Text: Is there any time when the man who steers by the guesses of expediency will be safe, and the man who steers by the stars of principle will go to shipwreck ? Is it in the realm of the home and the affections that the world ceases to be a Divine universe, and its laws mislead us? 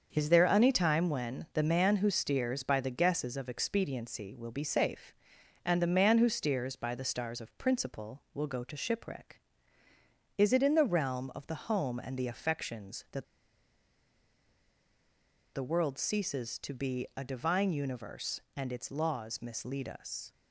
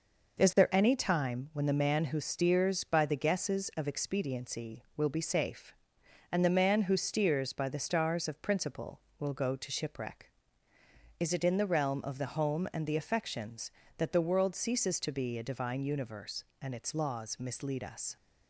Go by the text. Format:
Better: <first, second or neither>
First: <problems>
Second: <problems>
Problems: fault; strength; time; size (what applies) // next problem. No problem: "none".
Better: second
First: starts louder than the rest; until 1.1 s; 6.5 dB // pauses between "that" and "the"; strong; at 13.2 s; 2.2 s long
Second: none